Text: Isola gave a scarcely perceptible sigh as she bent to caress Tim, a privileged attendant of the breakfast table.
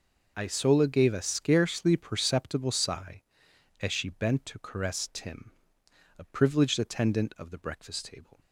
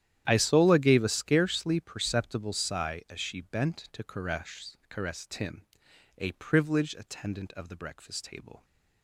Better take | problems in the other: first | starts louder than the rest; strong; until 1.2 s; 11 dB // says "caress" twice; at 4.8 s

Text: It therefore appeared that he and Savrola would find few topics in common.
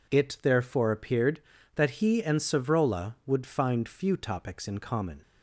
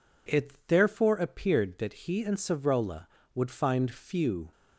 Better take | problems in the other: first | pauses between "It" and "therefore"; slight; at 0.5 s; 0.16 s long // stops before "topics in common"; at 4.5 s

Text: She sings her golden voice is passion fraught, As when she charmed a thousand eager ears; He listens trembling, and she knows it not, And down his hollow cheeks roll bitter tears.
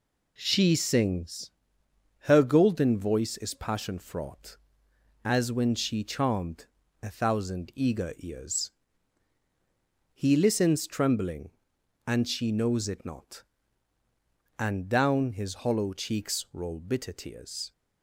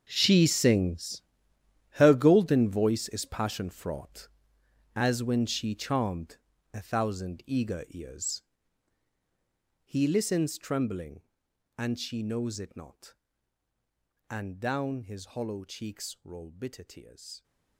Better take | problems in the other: first | gets quieter; strong; throughout; 16 dB // pauses between "sings" and "her"; noticeable; at 1.2 s; 0.78 s long; noticeable in the first // pauses between "charmed" and "a"; slight; at 6.3 s; 0.36 s long; slight in the first

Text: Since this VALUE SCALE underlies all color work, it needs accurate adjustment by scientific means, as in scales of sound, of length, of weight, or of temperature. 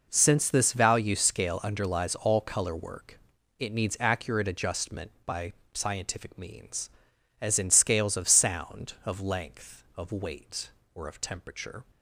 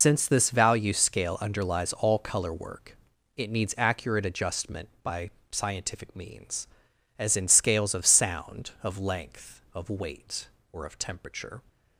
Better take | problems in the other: first | loses the start of "Since"; at 0.0 s; 125 ms // pauses between "by" and "scientific"; slight; at 5.2 s; 0.22 s long; slight in the first

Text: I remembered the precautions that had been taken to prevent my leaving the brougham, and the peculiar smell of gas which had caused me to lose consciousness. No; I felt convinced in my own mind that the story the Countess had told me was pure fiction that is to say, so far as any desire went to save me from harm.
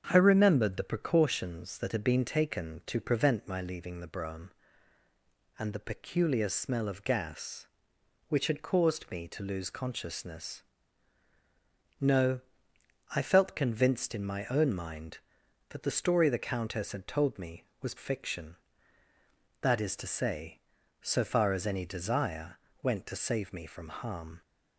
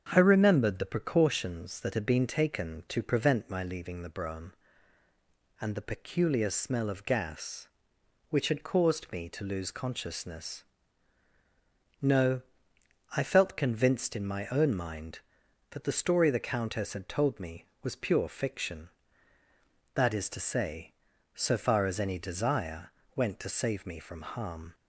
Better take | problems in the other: second | starts louder than the rest; strong; until 1.0 s; 7 dB; strong in the second // skips "pure"; at 17.9 s // pauses between "desire" and "went"; slight; at 22.5 s; 0.26 s long; slight in the second

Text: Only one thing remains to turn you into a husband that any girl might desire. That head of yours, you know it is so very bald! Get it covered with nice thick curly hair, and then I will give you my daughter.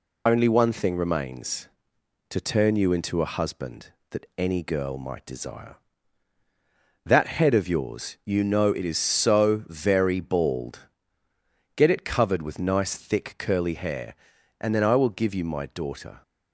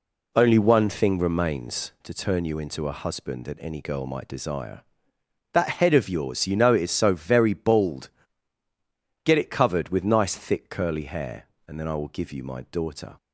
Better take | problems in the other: second | loses the start of "Only"; at 0.2 s; 55 ms

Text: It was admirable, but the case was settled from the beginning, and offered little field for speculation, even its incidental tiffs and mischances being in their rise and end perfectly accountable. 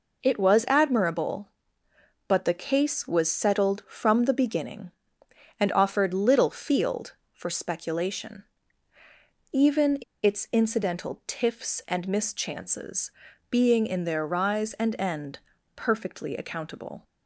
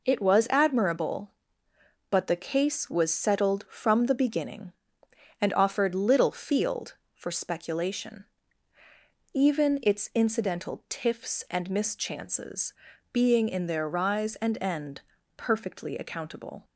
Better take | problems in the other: second | pauses between "even" and "its"; slight; at 9.9 s; 0.25 s long // pauses between "mischances" and "being"; at 13.1 s; 0.40 s long; also in the second // pauses between "end" and "perfectly"; slight; at 15.3 s; 0.36 s long; slight in the second

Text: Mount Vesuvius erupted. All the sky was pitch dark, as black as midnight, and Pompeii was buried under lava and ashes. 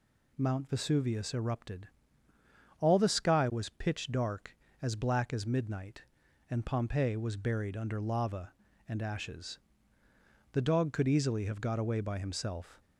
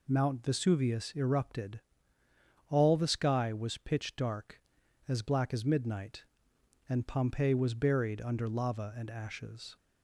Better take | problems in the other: second | goes on to say "The dog could easily have got away by himself"; strong; from 10.5 s on; 2.2 s long

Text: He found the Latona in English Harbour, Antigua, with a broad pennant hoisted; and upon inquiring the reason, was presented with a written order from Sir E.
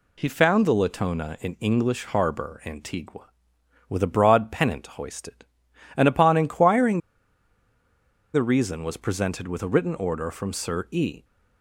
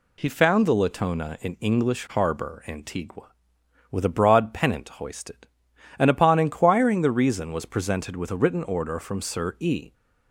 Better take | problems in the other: second | pauses between "inquiring" and "the"; strong; at 6.9 s; 1.3 s long

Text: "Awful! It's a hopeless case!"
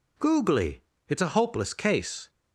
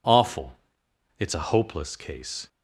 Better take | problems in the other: second | says "Googly" for "Awful"; at 0.1 s

